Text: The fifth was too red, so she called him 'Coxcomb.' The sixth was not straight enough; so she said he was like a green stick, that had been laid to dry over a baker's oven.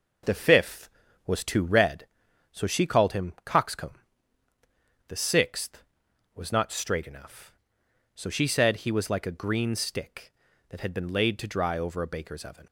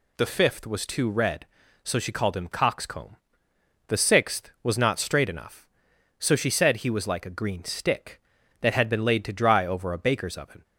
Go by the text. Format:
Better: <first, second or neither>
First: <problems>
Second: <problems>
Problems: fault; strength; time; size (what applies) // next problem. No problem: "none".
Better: neither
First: none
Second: none